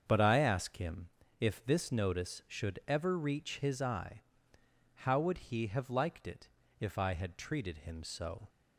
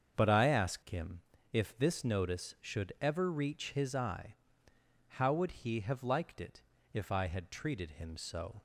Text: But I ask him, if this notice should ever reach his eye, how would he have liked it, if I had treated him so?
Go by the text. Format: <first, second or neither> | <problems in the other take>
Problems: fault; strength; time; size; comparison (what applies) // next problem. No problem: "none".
neither | starts louder than the rest; strong; the same in both